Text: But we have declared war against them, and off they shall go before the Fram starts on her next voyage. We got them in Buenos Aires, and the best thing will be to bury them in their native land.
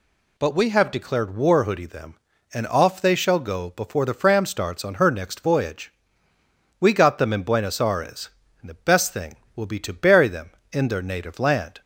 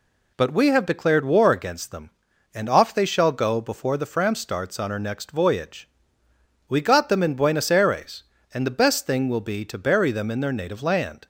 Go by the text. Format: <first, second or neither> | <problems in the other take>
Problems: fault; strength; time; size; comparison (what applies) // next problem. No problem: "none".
second | says "hoodie" for "against"; at 1.6 s